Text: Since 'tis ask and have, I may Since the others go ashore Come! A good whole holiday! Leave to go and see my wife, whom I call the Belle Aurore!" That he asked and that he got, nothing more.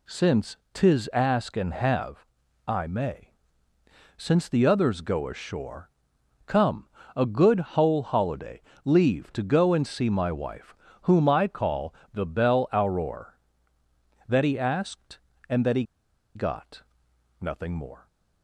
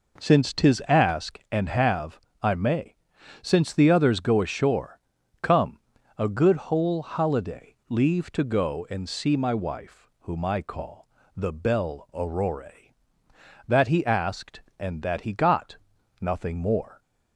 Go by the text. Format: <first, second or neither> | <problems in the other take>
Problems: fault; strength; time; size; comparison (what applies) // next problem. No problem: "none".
second | pauses between "Since" and "tis"; slight; at 0.5 s; 0.18 s long // pauses between "may" and "Since"; noticeable; at 3.3 s; 0.84 s long; noticeable in the second // pauses between "ashore" and "Come"; noticeable; at 5.8 s; 0.56 s long; also in the second // pauses between "good" and "whole"; slight; at 7.5 s; 0.16 s long // pauses between "call" and "the"; slight; at 11.9 s; 0.20 s long; slight in the second // pauses between "he" and "got"; noticeable; at 15.8 s; 0.52 s long